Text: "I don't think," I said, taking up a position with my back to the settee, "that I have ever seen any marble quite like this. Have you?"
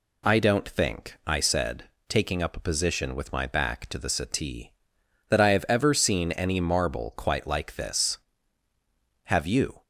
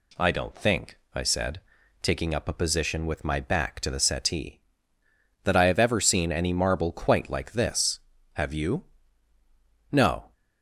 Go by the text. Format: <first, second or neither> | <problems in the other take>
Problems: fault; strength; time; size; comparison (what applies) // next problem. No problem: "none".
first | goes on to say "No"; slight; from 9.9 s on; 0.42 s long